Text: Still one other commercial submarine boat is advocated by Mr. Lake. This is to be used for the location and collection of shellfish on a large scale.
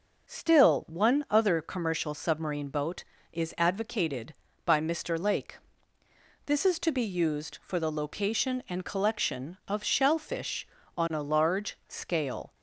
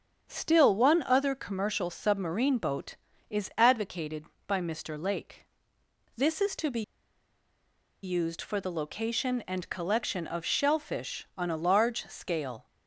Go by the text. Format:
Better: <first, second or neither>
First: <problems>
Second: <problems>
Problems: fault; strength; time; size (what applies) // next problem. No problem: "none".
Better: first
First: none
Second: starts louder than the rest; strong; until 1.3 s; 7.5 dB // pauses between "be" and "used"; at 6.8 s; 1.2 s long